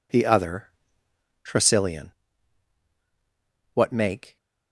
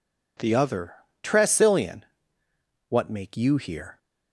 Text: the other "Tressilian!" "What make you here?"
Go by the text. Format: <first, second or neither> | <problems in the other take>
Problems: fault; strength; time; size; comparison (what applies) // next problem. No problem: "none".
second | pauses between "other" and "Tressilian"; noticeable; at 0.6 s; 0.76 s long; slight in the second // stops before "you here"; at 4.3 s